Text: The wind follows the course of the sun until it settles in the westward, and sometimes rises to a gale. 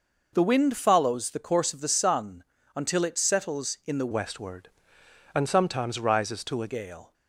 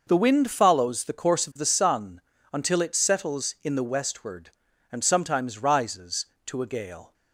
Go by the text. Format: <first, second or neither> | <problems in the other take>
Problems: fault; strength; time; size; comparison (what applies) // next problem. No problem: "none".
second | pauses between "sun" and "until"; slight; at 2.4 s; 0.32 s long; slight in the second // changes voice from "westward" to "a"; from 4.1 to 6.6 s; 2.5 s long